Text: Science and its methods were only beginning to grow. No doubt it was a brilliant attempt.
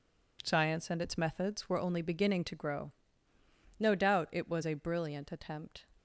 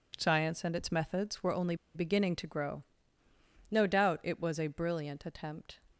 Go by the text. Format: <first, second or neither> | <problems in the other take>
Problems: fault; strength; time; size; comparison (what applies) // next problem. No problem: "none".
first | pauses between "only" and "beginning"; slight; at 1.7 s; 0.20 s long